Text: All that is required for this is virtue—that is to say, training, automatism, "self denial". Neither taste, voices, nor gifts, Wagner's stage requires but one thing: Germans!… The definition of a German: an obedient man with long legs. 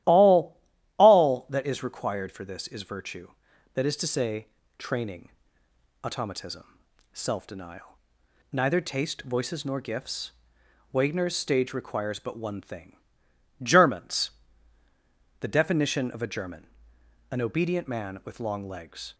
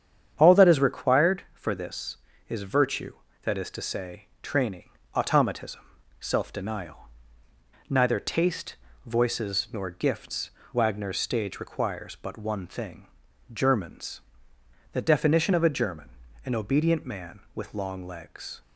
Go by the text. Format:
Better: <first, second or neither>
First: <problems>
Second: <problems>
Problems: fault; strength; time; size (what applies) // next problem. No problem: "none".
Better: second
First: starts louder than the rest; strong; until 1.4 s; 14 dB // says "All" twice; at 0.9 s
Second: starts louder than the rest; strong; until 1.3 s; 8.5 dB